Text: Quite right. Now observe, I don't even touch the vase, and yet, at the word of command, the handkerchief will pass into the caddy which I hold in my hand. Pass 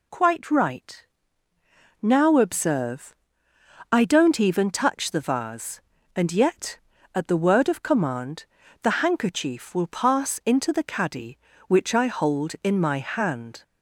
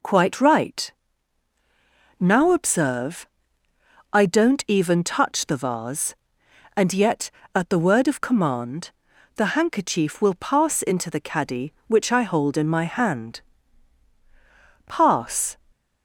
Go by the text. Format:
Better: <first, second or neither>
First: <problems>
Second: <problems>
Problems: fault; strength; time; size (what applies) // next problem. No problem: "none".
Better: second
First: stops before "Pass"; at 13.6 s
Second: none